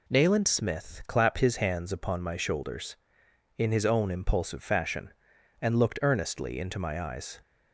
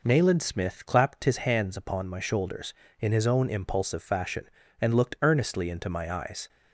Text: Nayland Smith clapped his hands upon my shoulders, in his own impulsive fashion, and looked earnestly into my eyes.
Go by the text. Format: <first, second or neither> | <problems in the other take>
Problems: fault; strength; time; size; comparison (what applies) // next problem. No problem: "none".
neither | none